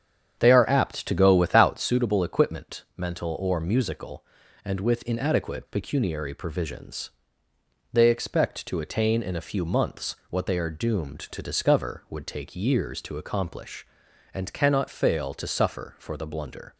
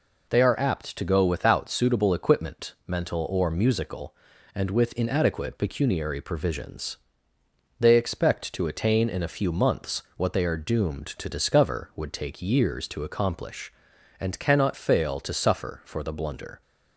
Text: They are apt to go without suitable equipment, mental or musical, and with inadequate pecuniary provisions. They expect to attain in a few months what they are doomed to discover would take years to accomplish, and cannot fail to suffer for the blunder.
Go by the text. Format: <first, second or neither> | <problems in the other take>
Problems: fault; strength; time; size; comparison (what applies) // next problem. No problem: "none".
second | starts louder than the rest; strong; until 2.0 s; 8 dB